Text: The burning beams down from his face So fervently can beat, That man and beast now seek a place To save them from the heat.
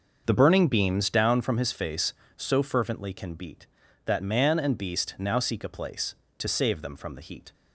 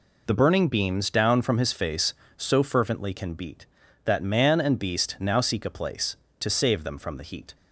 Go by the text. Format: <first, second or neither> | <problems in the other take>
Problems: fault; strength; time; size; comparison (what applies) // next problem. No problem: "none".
second | starts louder than the rest; until 1.4 s; 6.5 dB